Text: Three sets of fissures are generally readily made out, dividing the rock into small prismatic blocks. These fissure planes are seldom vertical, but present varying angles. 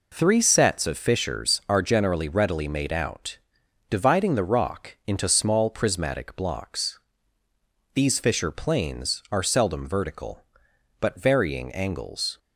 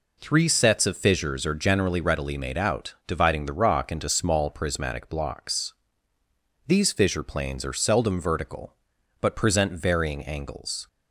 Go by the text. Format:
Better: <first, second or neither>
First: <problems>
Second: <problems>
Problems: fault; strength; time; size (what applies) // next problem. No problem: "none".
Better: second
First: skips "present"; at 11.1 s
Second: none